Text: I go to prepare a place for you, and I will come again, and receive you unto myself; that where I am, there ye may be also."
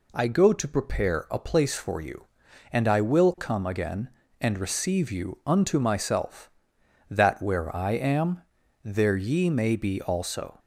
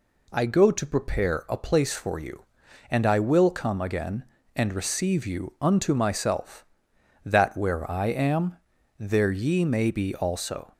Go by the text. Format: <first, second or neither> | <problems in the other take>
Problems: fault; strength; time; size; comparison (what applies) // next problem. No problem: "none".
neither | none